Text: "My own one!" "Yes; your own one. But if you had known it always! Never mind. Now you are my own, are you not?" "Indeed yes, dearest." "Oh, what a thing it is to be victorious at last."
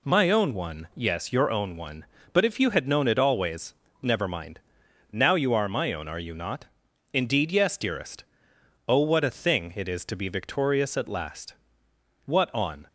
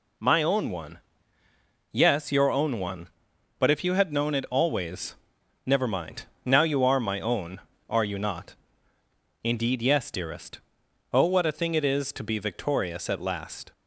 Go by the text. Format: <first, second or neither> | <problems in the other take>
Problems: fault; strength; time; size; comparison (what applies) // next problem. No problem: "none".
second | goes on to say "What on"; noticeable; from 12.2 s on; 0.62 s long